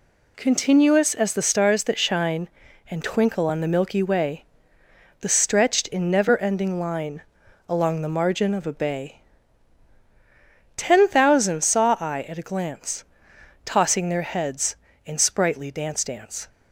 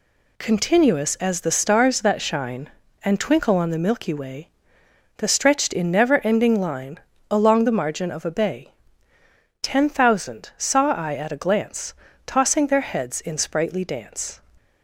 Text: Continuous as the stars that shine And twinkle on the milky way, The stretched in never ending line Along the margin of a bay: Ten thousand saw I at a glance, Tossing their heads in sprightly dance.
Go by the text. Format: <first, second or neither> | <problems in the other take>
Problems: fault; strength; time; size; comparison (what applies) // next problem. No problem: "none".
second | pauses between "line" and "Along"; noticeable; at 7.2 s; 0.46 s long; slight in the second // says "dance" twice; at 16.0 s